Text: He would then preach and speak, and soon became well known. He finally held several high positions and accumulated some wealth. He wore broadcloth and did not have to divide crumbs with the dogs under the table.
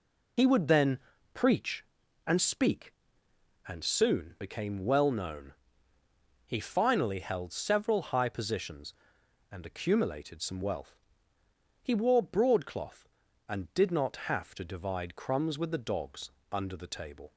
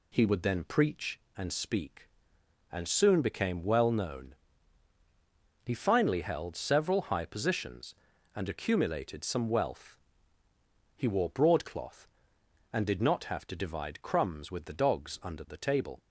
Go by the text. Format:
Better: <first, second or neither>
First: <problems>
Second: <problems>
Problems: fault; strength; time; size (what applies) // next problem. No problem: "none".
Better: second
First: loses the start of "He"; at 0.3 s; 60 ms // pauses between "then" and "preach"; slight; at 0.9 s; 0.36 s long // pauses between "dogs" and "under"; slight; at 16.3 s; 0.22 s long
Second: none